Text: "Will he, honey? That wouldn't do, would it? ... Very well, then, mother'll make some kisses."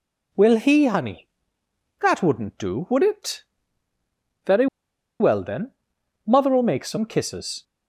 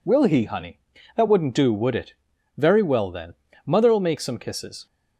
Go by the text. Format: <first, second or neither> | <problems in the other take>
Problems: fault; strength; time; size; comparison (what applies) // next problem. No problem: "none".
second | pauses between "Very" and "well"; noticeable; at 4.6 s; 0.54 s long